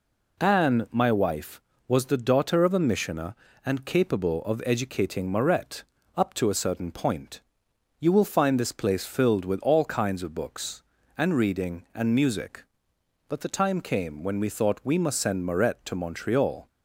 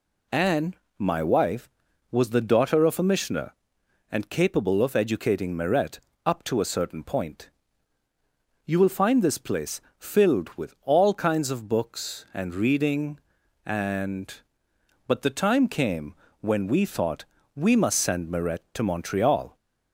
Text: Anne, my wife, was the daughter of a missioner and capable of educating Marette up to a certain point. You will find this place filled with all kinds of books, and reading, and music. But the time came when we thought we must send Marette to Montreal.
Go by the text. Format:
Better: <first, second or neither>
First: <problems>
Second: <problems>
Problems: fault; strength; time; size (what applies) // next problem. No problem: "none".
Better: first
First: pauses between "Marette" and "up"; slight; at 5.8 s; 0.34 s long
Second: pauses between "Marette" and "up"; slight; at 5.9 s; 0.26 s long // pauses between "place" and "filled"; slight; at 9.7 s; 0.18 s long // skips "music"; at 14.6 s // pauses between "came" and "when"; slight; at 16.1 s; 0.28 s long // pauses between "thought" and "we"; slight; at 17.2 s; 0.32 s long